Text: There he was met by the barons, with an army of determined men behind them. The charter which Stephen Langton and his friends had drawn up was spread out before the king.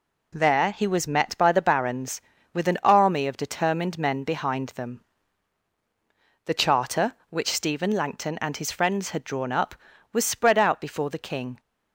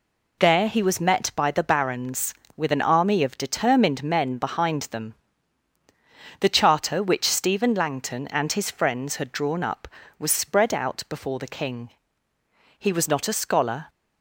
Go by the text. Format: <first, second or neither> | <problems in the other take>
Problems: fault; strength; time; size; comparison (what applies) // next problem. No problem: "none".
first | goes on to say "He was not a scholar"; noticeable; from 12.7 s on; 1.1 s long